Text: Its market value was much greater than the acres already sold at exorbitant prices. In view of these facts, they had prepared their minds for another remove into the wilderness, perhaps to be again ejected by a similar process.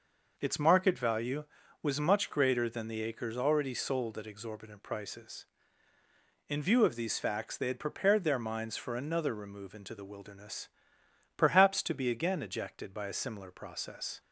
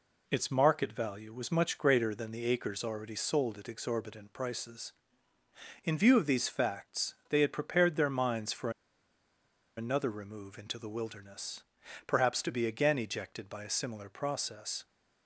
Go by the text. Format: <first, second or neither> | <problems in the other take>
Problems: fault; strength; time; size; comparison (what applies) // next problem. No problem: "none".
first | pauses between "for" and "another"; at 8.7 s; 1.0 s long